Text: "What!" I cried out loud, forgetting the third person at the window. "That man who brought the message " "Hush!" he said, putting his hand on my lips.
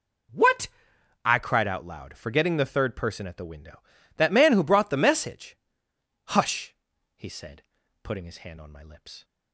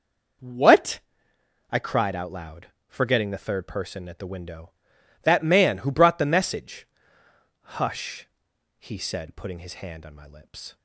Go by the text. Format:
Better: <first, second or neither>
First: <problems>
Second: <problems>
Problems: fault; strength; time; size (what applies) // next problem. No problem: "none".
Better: neither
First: none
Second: none